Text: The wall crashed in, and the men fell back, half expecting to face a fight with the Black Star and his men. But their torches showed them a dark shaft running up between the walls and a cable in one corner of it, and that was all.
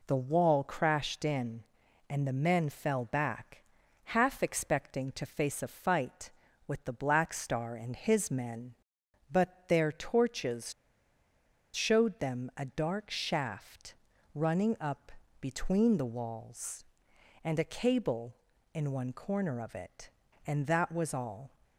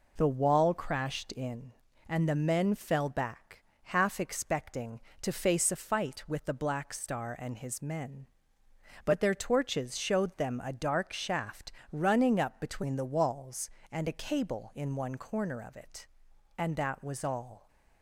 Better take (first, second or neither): second